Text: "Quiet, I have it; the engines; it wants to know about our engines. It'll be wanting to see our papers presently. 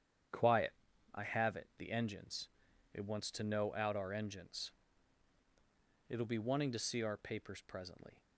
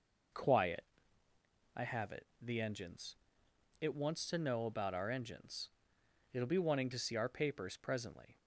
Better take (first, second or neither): second